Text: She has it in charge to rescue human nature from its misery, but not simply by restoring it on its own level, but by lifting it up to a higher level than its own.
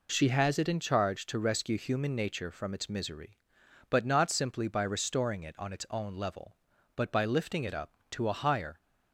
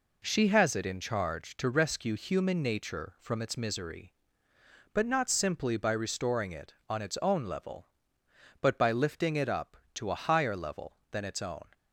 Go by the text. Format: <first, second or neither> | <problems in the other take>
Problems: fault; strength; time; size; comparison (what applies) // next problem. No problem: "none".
second | stops before "level than its own"; at 8.8 s